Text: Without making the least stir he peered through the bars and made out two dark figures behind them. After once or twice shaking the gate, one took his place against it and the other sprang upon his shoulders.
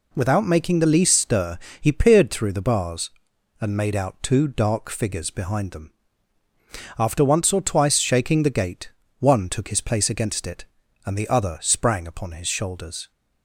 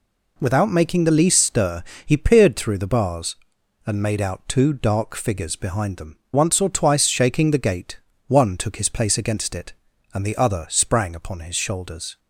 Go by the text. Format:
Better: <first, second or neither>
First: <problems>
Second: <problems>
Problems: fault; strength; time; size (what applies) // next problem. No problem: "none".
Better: first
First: pauses between "stir" and "he"; slight; at 1.5 s; 0.22 s long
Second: pauses between "stir" and "he"; slight; at 1.8 s; 0.22 s long // skips "After"; at 6.2 s